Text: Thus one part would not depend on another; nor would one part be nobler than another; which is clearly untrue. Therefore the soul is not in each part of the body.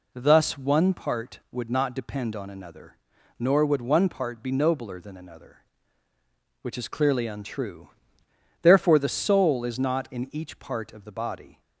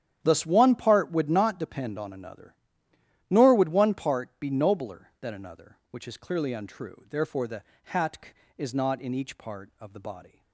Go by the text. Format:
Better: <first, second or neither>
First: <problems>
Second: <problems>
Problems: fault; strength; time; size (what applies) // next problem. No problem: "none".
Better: first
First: none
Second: starts louder than the rest; strong; until 1.2 s; 10 dB // says "hatk" for "soul"; at 7.8 s